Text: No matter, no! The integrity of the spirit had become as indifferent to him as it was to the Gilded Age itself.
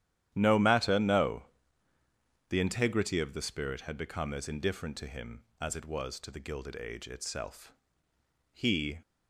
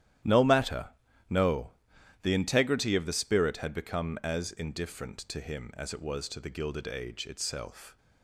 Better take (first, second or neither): second